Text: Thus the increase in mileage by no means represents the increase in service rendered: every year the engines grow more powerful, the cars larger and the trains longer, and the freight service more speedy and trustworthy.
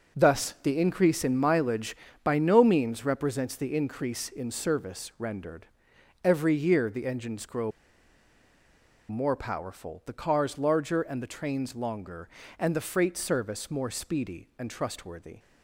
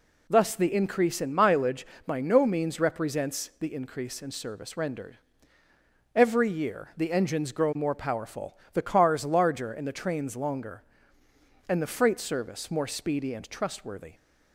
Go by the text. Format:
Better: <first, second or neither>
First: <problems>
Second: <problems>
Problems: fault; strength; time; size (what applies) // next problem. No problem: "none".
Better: second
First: pauses between "grow" and "more"; strong; at 7.7 s; 1.3 s long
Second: none